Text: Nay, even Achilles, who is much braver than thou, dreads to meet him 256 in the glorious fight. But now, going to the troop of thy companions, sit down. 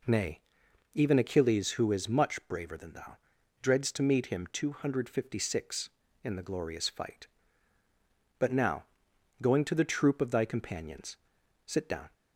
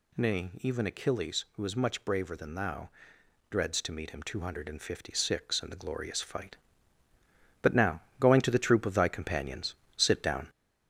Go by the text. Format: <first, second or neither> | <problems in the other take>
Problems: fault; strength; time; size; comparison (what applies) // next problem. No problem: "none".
first | gets louder; noticeable; throughout; 4 dB